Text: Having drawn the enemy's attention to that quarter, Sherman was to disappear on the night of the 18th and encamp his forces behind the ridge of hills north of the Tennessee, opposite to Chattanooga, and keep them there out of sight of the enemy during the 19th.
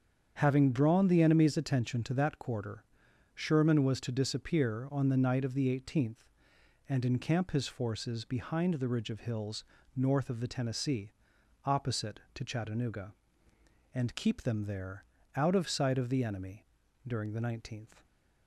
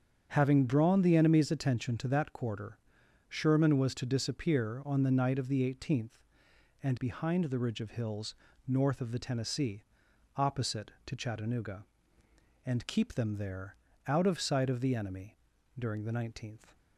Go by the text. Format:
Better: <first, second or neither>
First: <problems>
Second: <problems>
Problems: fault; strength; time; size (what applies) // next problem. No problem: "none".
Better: first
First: starts louder than the rest; strong; until 1.3 s; 7.5 dB // pauses between "hills" and "north"; slight; at 9.6 s; 0.31 s long // pauses between "there" and "out"; slight; at 15.0 s; 0.30 s long // pauses between "enemy" and "during"; at 16.6 s; 0.42 s long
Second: starts louder than the rest; strong; until 1.3 s; 7.5 dB // skips "encamp his forces"; at 6.9 s // pauses between "hills" and "north"; slight; at 8.3 s; 0.32 s long // pauses between "there" and "out"; slight; at 13.7 s; 0.30 s long // pauses between "enemy" and "during"; at 15.3 s; 0.42 s long